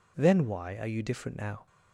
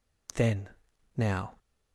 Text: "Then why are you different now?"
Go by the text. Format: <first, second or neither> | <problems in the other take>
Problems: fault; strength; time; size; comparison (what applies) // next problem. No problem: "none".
first | skips "why are you different"; at 0.9 s